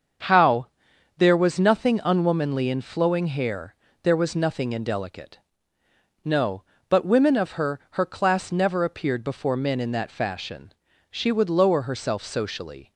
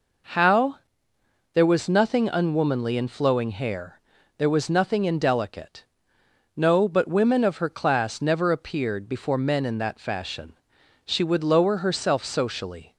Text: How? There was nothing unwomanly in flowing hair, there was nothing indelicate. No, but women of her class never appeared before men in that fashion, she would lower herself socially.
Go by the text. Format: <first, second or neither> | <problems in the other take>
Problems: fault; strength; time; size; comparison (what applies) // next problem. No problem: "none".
second | starts louder than the rest; until 1.7 s; 7 dB // says "her" twice; at 7.9 s